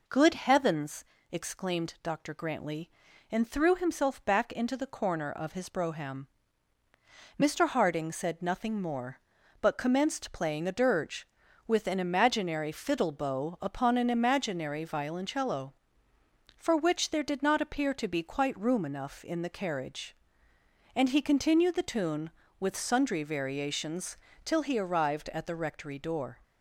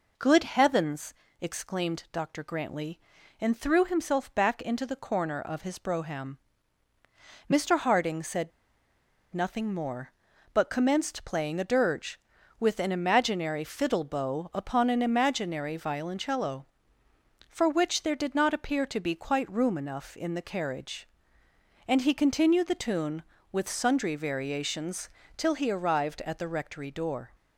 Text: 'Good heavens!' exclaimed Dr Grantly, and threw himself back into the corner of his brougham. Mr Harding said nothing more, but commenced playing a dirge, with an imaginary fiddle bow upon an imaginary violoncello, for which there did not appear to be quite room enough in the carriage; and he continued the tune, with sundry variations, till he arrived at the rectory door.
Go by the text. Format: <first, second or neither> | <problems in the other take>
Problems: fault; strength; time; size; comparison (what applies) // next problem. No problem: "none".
first | pauses between "said" and "nothing"; noticeable; at 8.5 s; 0.82 s long